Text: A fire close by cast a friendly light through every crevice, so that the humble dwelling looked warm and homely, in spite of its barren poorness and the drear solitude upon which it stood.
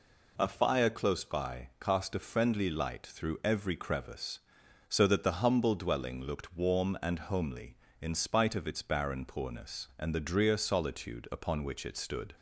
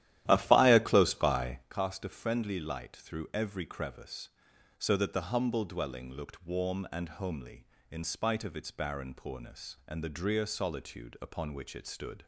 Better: first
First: none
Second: starts louder than the rest; strong; until 1.7 s; 13 dB

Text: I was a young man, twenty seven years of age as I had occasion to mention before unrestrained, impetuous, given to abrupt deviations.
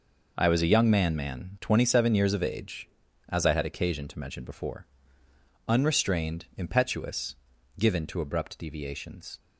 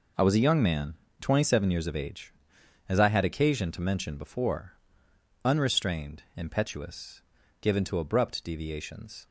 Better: second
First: says "man" twice; at 1.1 s // pauses between "before" and "unrestrained"; noticeable; at 4.8 s; 0.84 s long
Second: pauses between "before" and "unrestrained"; noticeable; at 4.7 s; 0.70 s long

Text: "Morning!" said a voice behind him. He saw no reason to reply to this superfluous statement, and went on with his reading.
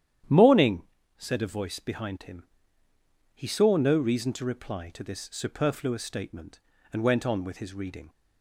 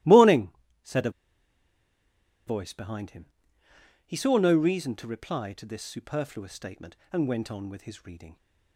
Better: first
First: starts louder than the rest; strong; until 1.6 s; 10 dB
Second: starts louder than the rest; strong; until 2.7 s; 16.5 dB // pauses between "a" and "voice"; strong; at 1.1 s; 1.3 s long

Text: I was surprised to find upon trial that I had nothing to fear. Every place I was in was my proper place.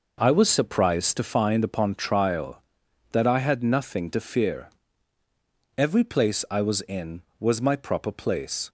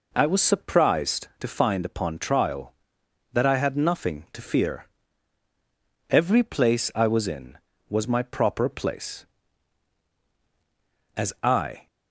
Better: first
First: none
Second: goes on to say "As I"; noticeable; from 11.1 s on; 0.70 s long

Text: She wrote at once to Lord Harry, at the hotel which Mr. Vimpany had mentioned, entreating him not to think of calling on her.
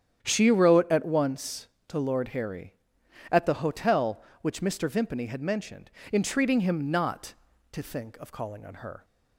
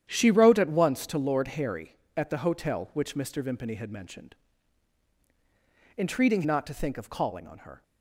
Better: first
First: starts louder than the rest; strong; until 1.2 s; 9 dB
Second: starts louder than the rest; strong; until 1.1 s; 9.5 dB // skips "him"; at 6.4 s

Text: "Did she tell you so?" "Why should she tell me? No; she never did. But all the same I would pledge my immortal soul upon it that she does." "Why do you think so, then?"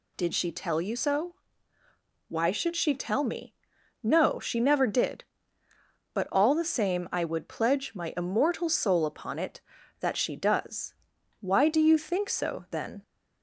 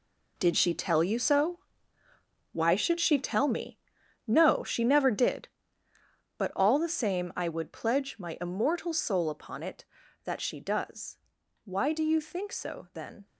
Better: first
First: none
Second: gets quieter; strong; throughout; 11.5 dB

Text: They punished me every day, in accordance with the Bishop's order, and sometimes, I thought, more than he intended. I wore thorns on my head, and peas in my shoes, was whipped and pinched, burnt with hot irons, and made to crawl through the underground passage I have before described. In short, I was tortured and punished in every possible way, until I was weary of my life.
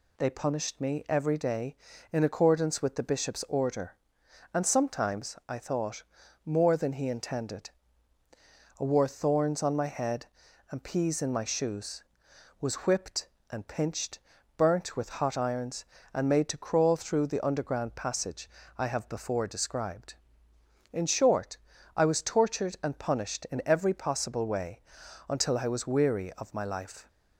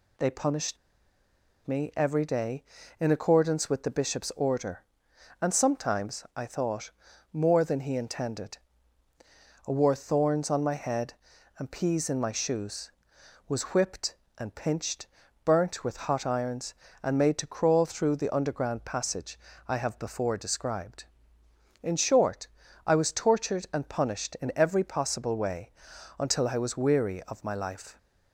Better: first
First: pauses between "passage" and "I"; slight; at 18.4 s; 0.29 s long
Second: pauses between "punished" and "me"; noticeable; at 0.7 s; 0.90 s long // pauses between "passage" and "I"; slight; at 19.3 s; 0.28 s long

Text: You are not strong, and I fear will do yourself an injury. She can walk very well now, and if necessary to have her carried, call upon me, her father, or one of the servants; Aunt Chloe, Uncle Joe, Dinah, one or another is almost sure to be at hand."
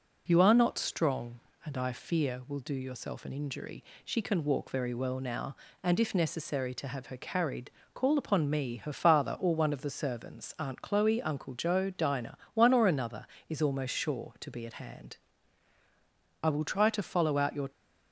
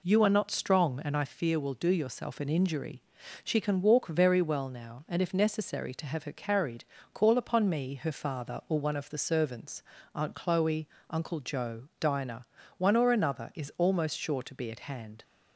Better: second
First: goes on to say "I will try to follow out your"; noticeable; from 16.4 s on; 1.2 s long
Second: none

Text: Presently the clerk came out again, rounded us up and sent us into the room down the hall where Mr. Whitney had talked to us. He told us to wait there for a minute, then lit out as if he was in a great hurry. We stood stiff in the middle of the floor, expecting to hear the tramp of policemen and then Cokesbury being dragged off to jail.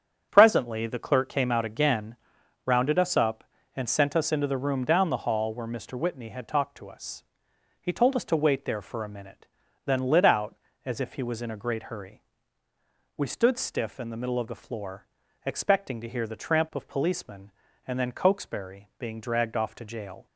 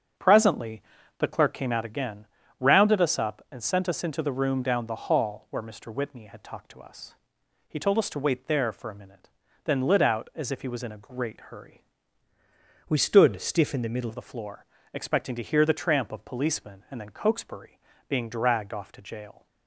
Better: first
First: starts louder than the rest; strong; until 1.3 s; 8 dB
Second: starts louder than the rest; strong; until 1.5 s; 8 dB // pauses between "Presently" and "the"; at 0.8 s; 0.38 s long // changes voice from "We" to "middle"; from 12.8 to 14.1 s; 1.3 s long // pauses between "Cokesbury" and "being"; slight; at 17.7 s; 0.30 s long

